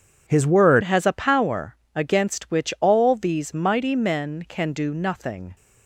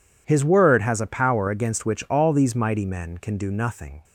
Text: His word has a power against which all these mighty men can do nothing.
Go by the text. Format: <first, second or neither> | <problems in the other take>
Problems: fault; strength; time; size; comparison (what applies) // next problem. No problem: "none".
second | changes voice at "has"; from 0.8 s on; 4.7 s long // pauses between "power" and "against"; slight; at 1.7 s; 0.18 s long